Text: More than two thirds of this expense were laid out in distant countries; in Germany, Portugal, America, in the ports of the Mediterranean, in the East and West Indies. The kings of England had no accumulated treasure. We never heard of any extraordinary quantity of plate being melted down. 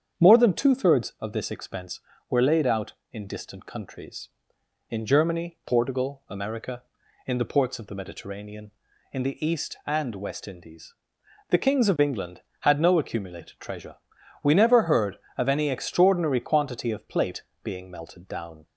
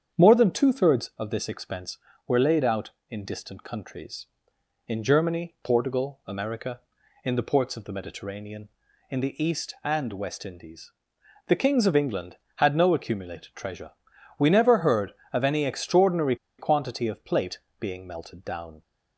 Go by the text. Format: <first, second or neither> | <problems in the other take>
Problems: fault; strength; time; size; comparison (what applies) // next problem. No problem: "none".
first | starts louder than the rest; strong; until 1.2 s; 8 dB; strong in the first // pauses between "extraordinary" and "quantity"; slight; at 16.3 s; 0.23 s long // pauses between "plate" and "being"; slight; at 17.5 s; 0.18 s long; slight in the first